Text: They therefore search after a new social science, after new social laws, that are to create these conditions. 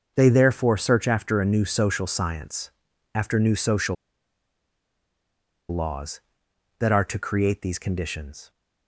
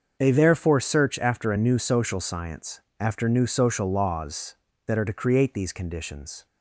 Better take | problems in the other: second | starts louder than the rest; until 1.1 s; 6.5 dB; also in the second // pauses between "social" and "laws"; strong; at 3.9 s; 1.7 s long

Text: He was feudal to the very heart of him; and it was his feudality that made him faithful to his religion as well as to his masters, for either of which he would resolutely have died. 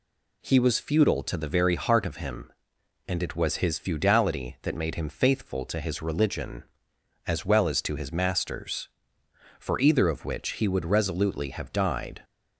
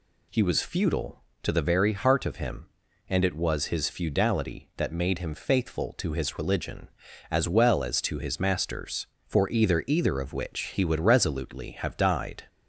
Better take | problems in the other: first | says "either" twice; at 9.8 s

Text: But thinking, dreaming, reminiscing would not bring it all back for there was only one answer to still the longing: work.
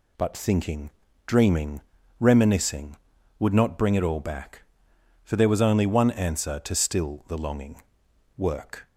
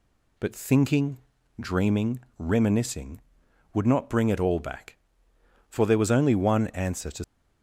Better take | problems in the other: first | stops before "still the longing work"; at 7.2 s

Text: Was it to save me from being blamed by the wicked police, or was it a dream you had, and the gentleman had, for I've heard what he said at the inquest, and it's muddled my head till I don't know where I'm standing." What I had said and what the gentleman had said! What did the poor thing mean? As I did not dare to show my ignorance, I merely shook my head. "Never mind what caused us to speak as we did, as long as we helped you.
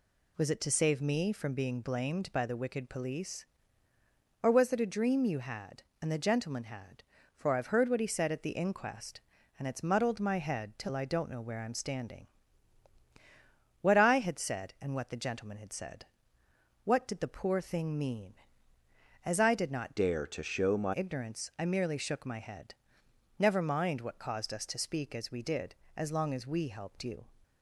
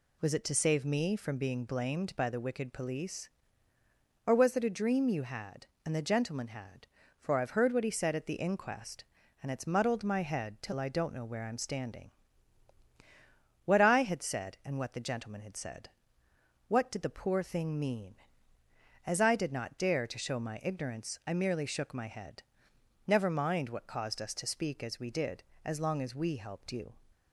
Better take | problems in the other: second | changes voice from "dare" to "my"; from 19.9 to 20.9 s; 1.0 s long

